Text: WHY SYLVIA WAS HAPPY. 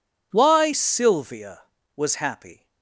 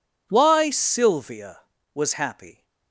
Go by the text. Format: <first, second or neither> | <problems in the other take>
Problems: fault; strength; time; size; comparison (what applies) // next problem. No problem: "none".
neither | none